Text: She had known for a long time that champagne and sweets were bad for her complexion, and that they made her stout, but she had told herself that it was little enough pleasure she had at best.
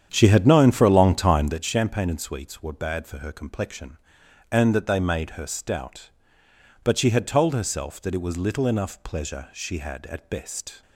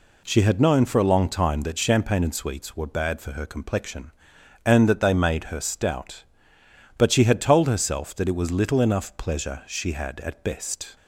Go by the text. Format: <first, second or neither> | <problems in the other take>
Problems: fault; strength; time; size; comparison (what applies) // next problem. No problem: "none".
second | starts louder than the rest; strong; until 1.6 s; 9 dB